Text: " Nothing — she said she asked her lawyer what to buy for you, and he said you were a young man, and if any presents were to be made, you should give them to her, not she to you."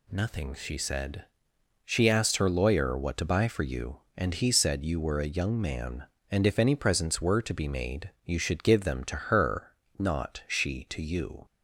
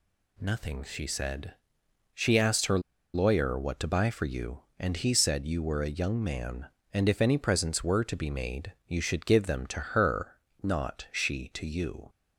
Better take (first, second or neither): first